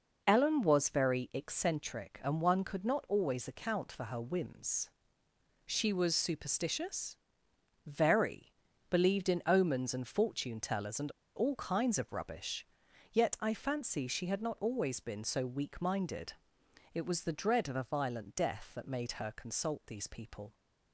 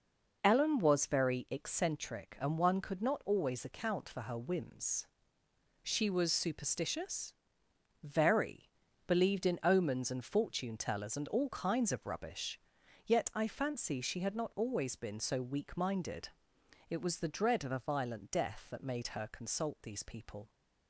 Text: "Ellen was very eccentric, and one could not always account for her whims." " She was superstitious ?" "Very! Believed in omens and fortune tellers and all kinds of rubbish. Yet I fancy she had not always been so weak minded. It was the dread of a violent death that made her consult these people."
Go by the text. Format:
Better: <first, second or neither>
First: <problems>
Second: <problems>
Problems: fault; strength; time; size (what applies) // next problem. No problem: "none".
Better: second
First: starts louder than the rest; until 1.2 s; 6.5 dB // pauses between "and" and "all"; slight; at 11.1 s; 0.25 s long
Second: starts louder than the rest; until 1.4 s; 6.5 dB